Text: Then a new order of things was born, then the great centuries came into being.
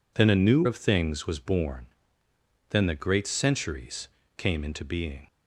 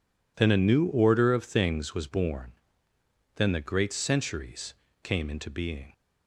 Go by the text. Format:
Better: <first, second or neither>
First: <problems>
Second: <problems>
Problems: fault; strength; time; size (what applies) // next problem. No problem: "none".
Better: second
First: skips "order"; at 0.6 s // pauses between "centuries" and "came"; slight; at 4.0 s; 0.30 s long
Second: pauses between "centuries" and "came"; slight; at 4.7 s; 0.30 s long